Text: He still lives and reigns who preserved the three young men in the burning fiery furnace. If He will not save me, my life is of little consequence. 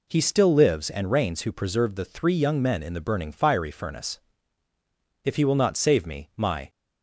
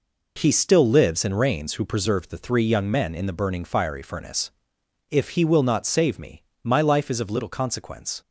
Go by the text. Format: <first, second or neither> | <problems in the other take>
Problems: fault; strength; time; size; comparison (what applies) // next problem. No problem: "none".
second | stops before "life is of little consequence"; at 6.7 s